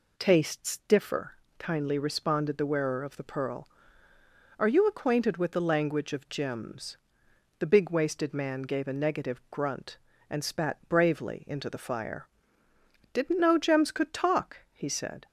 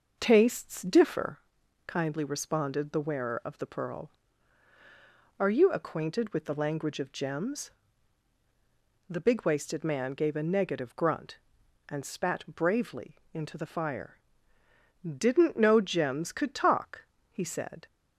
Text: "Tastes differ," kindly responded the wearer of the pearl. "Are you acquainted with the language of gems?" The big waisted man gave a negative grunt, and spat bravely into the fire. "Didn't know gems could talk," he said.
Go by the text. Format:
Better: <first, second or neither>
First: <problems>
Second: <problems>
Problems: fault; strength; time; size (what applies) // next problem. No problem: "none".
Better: first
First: none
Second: starts louder than the rest; noticeable; until 1.4 s; 6 dB // pauses between "bravely" and "into"; slight; at 13.1 s; 0.16 s long